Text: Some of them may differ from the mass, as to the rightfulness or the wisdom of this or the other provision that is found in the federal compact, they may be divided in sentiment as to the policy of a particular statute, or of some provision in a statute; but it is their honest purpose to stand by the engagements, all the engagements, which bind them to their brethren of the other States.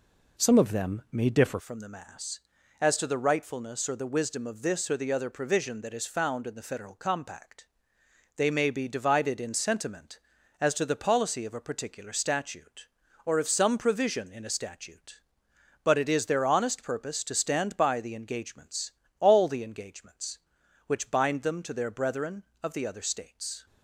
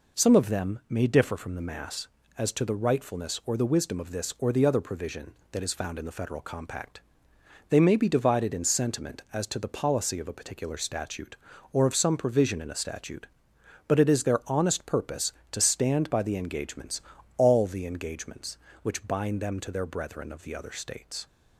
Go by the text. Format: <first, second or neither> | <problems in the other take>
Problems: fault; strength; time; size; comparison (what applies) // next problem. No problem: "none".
second | changes voice at "from"; from 1.5 s on; 22.1 s long